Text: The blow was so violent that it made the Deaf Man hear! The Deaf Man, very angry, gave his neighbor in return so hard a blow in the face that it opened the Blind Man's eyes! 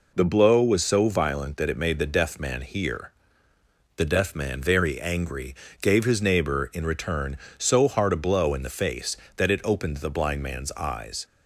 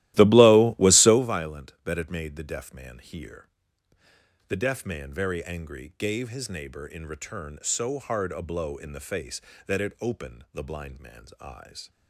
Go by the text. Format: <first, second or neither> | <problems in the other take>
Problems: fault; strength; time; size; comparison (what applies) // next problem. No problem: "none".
first | starts louder than the rest; strong; until 1.3 s; 15.5 dB